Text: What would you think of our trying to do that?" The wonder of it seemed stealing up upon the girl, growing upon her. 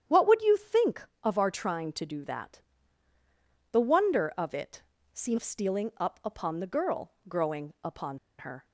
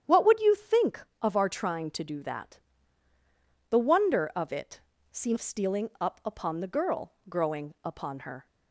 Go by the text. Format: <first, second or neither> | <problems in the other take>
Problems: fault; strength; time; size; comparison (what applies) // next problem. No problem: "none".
second | starts louder than the rest; strong; until 1.3 s; 9.5 dB; strong in the second // pauses between "it" and "seemed"; slight; at 4.8 s; 0.32 s long; slight in the second // pauses between "upon" and "her"; slight; at 8.1 s; 0.20 s long